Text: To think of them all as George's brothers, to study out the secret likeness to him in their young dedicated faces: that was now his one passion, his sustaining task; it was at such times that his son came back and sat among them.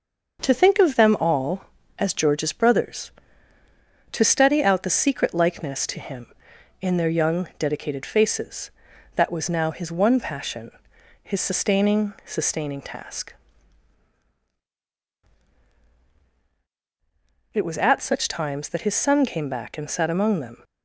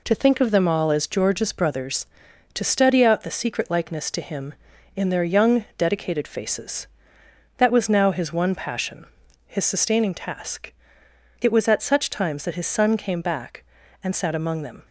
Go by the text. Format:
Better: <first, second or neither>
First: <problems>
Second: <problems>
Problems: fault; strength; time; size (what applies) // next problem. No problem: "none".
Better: second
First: starts louder than the rest; until 1.4 s; 6.5 dB // says "sustaining" twice; at 12.2 s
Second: none